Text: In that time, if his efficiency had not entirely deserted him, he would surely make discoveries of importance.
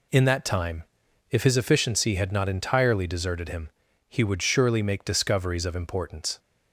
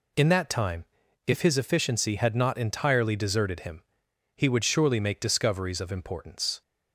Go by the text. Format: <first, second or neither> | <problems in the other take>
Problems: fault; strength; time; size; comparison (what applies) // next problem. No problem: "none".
neither | none